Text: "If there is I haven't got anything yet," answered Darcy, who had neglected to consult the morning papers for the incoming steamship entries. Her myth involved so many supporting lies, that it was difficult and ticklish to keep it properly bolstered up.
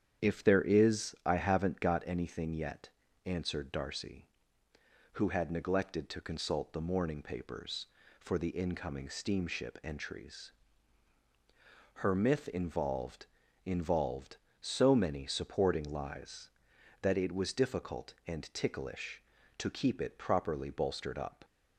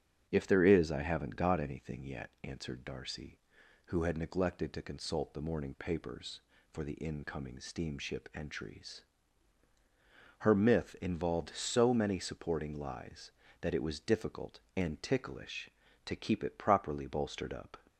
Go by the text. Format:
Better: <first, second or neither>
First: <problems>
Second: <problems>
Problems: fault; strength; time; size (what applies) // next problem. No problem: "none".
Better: second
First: starts louder than the rest; strong; until 1.2 s; 8.5 dB // says "involved" twice; at 13.6 s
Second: starts louder than the rest; strong; until 1.3 s; 8 dB